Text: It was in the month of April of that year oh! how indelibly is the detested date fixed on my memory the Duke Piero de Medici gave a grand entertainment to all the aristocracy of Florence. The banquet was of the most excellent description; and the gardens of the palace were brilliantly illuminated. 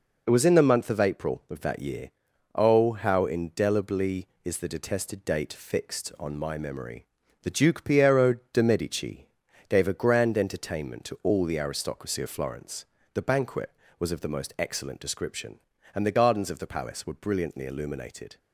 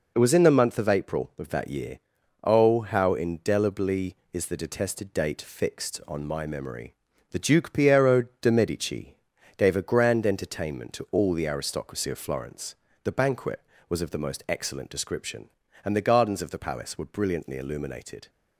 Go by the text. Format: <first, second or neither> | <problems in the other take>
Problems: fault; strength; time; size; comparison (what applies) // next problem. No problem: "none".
neither | pauses between "year" and "oh"; the same in both // pauses between "memory" and "the"; slight; the same in both // pauses between "Piero" and "de"; slight; the same in both // pauses between "Medici" and "gave"; the same in both